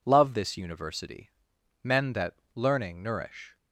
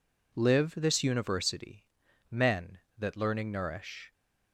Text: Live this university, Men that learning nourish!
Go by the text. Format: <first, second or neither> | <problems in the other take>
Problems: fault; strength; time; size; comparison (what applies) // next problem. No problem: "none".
second | says "Love" for "Live"; at 0.0 s // pauses between "that" and "learning"; slight; at 2.3 s; 0.18 s long